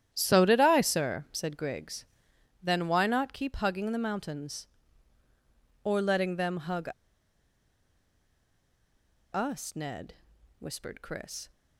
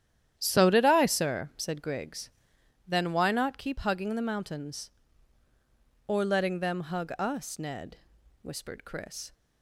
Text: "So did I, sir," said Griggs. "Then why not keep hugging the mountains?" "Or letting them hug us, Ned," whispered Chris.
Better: second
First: starts louder than the rest; strong; until 1.1 s; 10.5 dB // pauses between "hug" and "us"; strong; at 6.8 s; 2.4 s long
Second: starts louder than the rest; strong; until 1.3 s; 10.5 dB

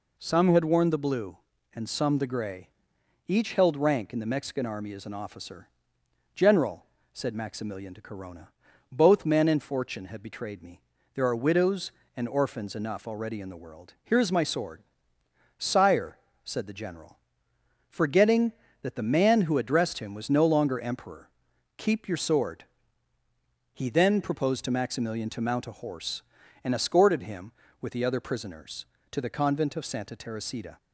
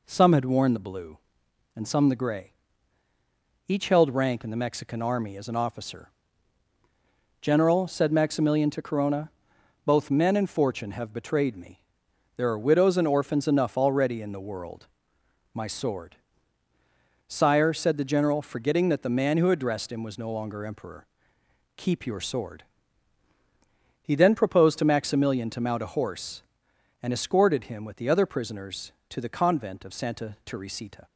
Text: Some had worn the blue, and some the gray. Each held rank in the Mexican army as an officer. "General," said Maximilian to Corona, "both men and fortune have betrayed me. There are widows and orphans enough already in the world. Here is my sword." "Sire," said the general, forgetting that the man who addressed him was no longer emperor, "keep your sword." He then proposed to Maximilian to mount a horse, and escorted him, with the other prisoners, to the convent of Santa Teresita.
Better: first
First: none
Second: skips "Here is"; at 15.2 s

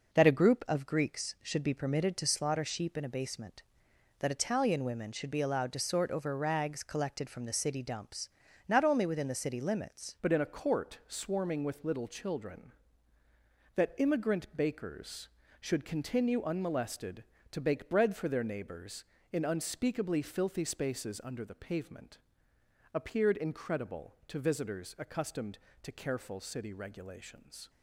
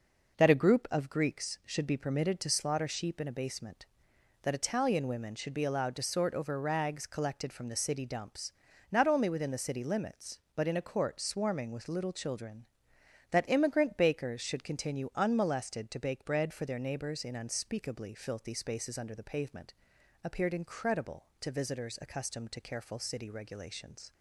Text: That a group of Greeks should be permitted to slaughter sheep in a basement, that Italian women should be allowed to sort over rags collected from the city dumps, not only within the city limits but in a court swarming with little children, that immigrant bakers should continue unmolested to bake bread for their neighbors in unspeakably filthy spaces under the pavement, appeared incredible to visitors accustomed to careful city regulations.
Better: second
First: changes voice at "but"; from 10.2 s on; 17.4 s long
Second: none

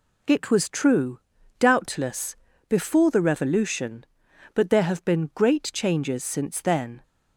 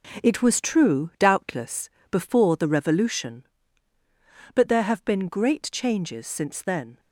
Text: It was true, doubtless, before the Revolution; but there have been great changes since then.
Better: first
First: none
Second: gets quieter; strong; throughout; 8 dB

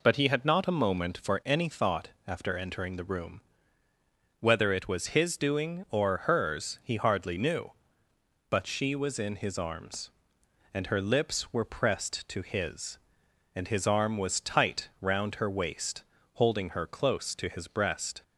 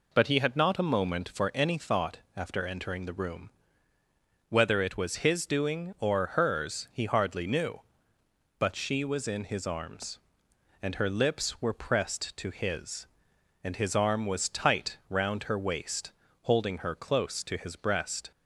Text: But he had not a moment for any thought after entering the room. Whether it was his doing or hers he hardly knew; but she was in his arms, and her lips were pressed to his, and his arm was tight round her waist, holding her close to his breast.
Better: neither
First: pauses between "thought" and "after"; slight; at 2.0 s; 0.18 s long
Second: pauses between "thought" and "after"; slight; at 2.1 s; 0.18 s long

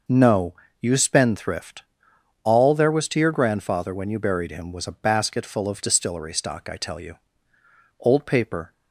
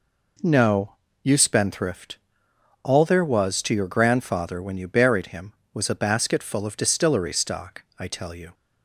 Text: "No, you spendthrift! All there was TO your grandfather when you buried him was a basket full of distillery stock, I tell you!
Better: second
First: goes on to say "Old paper"; noticeable; from 7.9 s on; 0.74 s long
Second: none

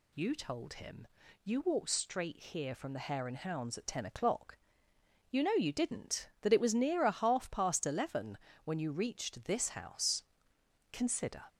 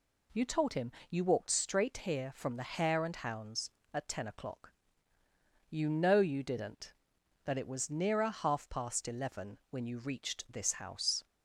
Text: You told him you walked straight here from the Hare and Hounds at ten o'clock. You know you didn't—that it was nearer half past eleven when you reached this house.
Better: second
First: pauses between "him" and "you"; slight; at 1.0 s; 0.36 s long // pauses between "eleven" and "when"; slight; at 8.3 s; 0.26 s long // goes on to say "Consider"; from 10.9 s on; 0.50 s long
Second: pauses between "him" and "you"; slight; at 0.9 s; 0.16 s long

